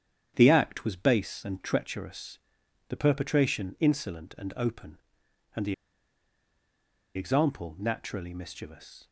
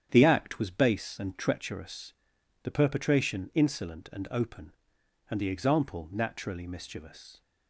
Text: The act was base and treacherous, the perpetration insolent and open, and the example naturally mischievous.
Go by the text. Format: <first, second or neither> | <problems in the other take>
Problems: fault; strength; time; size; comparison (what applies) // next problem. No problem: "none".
second | starts louder than the rest; strong; until 1.3 s; 9 dB; strong in the second // pauses between "the" and "example"; strong; at 5.7 s; 1.4 s long